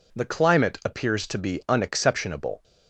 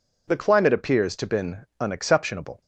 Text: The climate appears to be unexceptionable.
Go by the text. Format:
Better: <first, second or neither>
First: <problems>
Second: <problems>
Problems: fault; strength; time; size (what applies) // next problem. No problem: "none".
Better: first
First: none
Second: says "been" for "be"; at 1.2 s